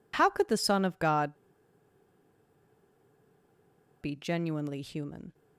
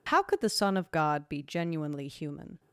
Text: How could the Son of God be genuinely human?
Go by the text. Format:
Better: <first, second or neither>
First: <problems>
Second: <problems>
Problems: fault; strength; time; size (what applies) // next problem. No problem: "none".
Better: second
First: pauses between "God" and "be"; strong; at 1.3 s; 2.6 s long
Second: none